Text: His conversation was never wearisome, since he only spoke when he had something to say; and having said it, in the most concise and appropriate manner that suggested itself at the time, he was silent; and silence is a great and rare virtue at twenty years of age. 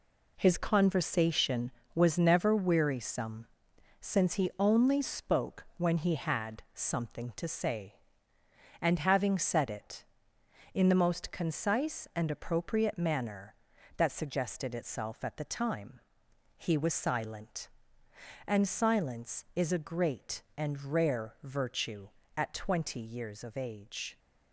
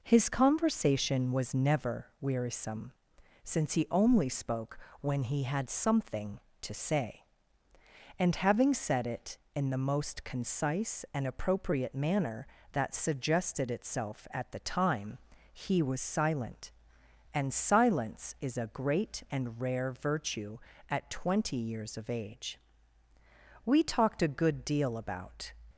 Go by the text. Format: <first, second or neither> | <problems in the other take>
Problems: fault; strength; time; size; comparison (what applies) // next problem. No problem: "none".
first | pauses between "spoke" and "when"; slight; at 4.7 s; 0.24 s long // goes on to say "We talked a good deal about"; strong; from 23.6 s on; 1.8 s long